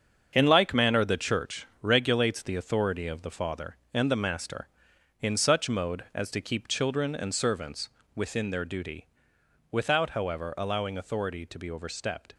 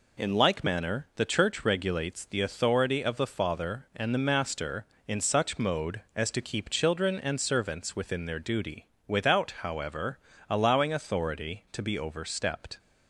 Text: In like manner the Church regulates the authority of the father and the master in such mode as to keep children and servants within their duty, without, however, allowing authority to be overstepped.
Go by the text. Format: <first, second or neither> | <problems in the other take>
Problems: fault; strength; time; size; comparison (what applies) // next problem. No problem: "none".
second | gets quieter; strong; throughout; 8 dB // pauses between "servants" and "within"; slight; at 7.8 s; 0.28 s long